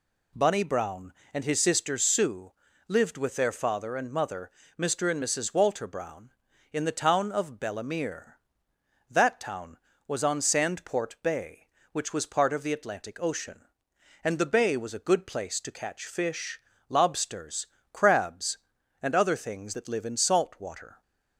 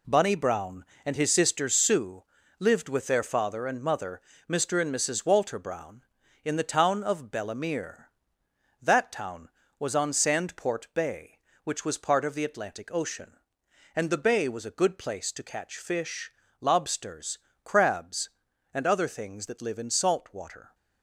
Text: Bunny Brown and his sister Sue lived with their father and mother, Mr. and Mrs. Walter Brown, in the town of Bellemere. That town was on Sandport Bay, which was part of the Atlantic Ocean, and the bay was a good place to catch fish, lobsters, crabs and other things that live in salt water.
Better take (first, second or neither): first